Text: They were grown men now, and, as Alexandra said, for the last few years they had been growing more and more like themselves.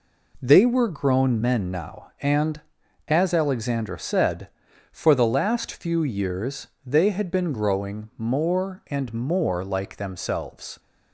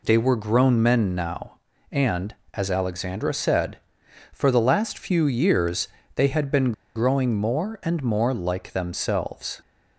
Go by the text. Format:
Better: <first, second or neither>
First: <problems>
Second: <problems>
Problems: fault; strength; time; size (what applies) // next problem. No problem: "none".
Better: first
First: pauses between "years" and "they"; slight; at 6.6 s; 0.18 s long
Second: pauses between "years" and "they"; slight; at 5.8 s; 0.28 s long // pauses between "been" and "growing"; slight; at 6.7 s; 0.23 s long